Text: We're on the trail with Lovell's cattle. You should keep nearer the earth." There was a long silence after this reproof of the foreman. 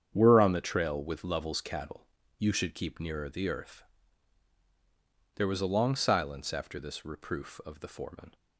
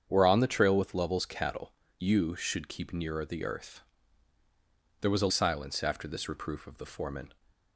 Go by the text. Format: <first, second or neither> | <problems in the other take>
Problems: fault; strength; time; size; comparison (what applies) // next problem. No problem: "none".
first | starts louder than the rest; strong; until 1.1 s; 7.5 dB; strong in the first // skips "long"; at 5.3 s